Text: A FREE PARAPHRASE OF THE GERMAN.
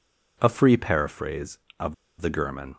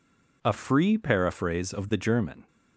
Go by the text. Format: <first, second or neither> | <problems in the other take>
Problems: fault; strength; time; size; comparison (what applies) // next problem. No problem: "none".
second | pauses between "OF" and "THE"; slight; at 1.9 s; 0.26 s long